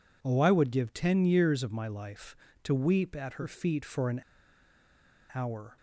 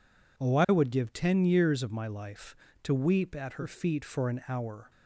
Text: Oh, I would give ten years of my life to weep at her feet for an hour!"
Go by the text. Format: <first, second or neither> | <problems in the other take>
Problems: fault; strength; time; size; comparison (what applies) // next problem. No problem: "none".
second | pauses between "an" and "hour"; at 4.2 s; 1.1 s long